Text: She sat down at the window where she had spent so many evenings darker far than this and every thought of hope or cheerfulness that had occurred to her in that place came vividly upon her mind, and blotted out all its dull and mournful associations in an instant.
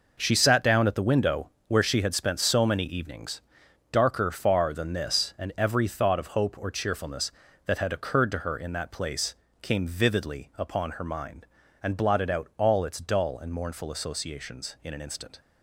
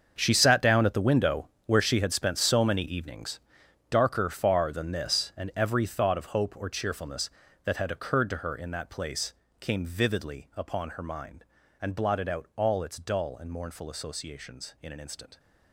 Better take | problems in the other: first | gets quieter; strong; throughout; 14.5 dB // pauses between "window" and "where"; slight; at 1.4 s; 0.20 s long; slight in the first // pauses between "evenings" and "darker"; noticeable; at 3.3 s; 0.52 s long; noticeable in the first // pauses between "place" and "came"; slight; at 9.3 s; 0.26 s long; slight in the first

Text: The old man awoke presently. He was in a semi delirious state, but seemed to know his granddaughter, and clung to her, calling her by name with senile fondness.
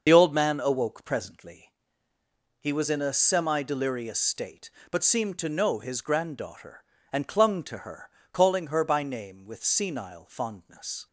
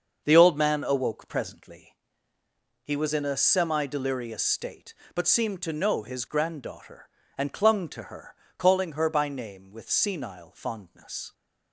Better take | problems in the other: second | loses the start of "The"; at 0.0 s; 55 ms // starts louder than the rest; until 1.0 s; 6 dB; also in the second

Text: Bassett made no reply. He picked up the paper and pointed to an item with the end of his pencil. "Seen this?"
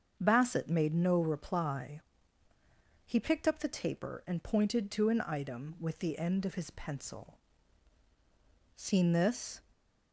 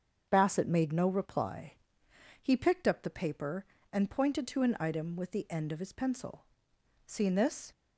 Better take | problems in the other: second | starts louder than the rest; strong; until 1.2 s; 7 dB; strong in the second // says "taper" for "paper"; at 3.6 s // stays silent after the last word; slight; from 9.6 s on; 0.5 s long

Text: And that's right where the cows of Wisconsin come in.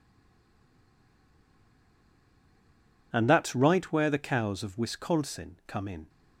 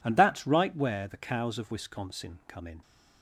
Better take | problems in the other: second | stays silent before the first word; strong; until 3.1 s; 3.1 s long

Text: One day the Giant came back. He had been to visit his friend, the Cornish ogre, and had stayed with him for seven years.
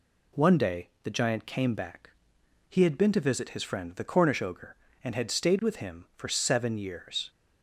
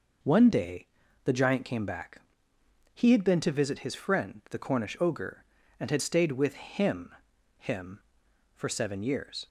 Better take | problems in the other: first | pauses between "day" and "the"; at 0.8 s; 0.40 s long; slight in the first // says "him" twice; at 7.5 s

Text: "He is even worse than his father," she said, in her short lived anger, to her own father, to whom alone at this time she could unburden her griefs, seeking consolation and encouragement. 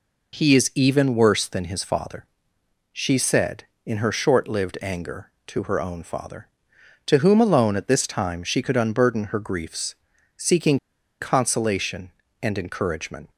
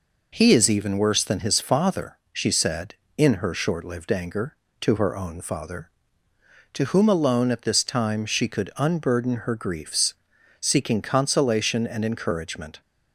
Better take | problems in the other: second | pauses between "seeking" and "consolation"; at 10.7 s; 0.44 s long

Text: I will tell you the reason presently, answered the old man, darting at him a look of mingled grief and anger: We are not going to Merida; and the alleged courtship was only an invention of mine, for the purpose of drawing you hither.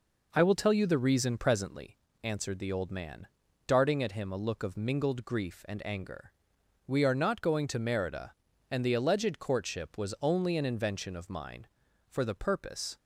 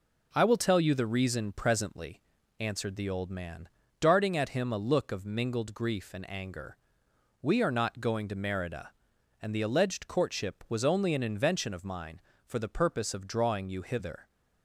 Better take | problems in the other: second | stops before "of drawing you hither"; at 12.9 s

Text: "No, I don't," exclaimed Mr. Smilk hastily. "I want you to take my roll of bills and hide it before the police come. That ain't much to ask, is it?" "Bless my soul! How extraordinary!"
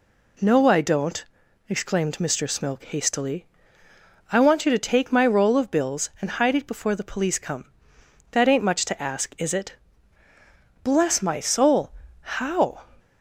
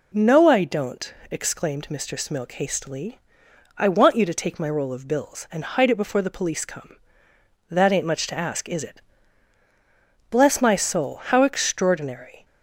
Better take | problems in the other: second | stops before "extraordinary"; at 12.9 s

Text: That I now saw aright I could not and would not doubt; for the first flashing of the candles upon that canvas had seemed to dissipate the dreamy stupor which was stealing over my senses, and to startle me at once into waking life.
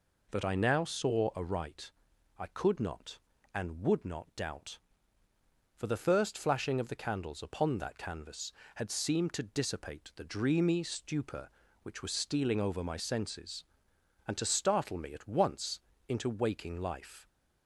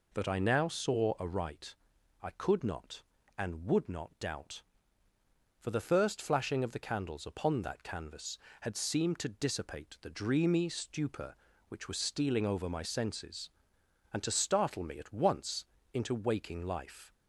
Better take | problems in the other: neither | pauses between "aright" and "I"; noticeable; the same in both // pauses between "once" and "into"; slight; the same in both

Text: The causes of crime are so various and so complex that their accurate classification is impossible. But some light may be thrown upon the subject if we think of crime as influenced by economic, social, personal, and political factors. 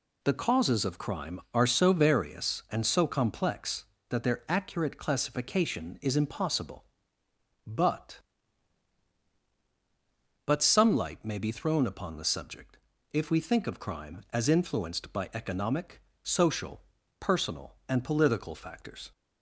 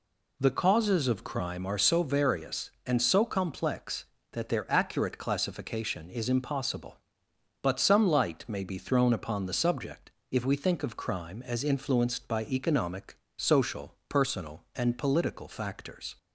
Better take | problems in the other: second | says "But" twice; at 10.4 s // pauses between "subject" and "if"; slight; at 12.7 s; 0.34 s long; slight in the second

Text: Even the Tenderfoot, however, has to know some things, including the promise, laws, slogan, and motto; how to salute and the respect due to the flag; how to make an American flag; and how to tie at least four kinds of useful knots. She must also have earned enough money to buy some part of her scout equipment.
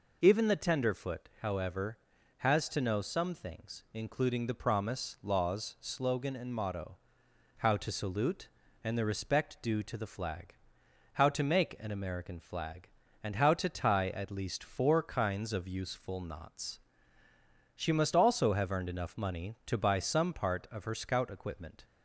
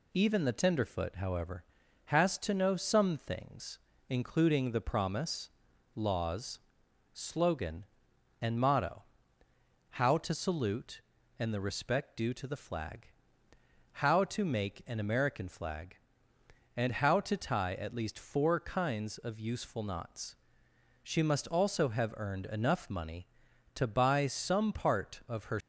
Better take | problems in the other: first | stops before "scout equipment"; at 25.6 s

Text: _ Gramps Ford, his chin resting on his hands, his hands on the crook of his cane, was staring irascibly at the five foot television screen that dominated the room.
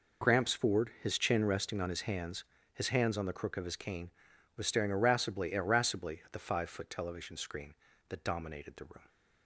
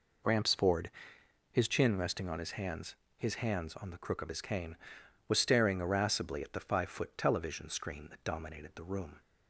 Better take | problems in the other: second | says "irascibly" twice; at 5.5 s

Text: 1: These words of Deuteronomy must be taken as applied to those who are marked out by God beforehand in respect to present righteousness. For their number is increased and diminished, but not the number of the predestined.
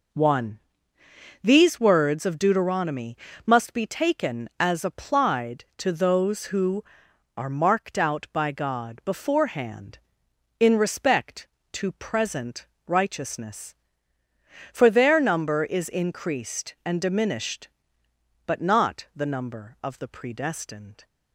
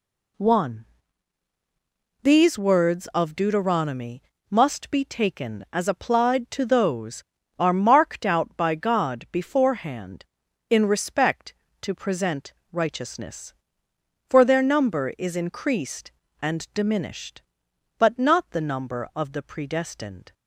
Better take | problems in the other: first | pauses between "Deuteronomy" and "must"; slight; at 4.2 s; 0.30 s long; slight in the first // skips "who"; at 7.3 s // pauses between "present" and "righteousness"; slight; at 12.5 s; 0.18 s long; slight in the first

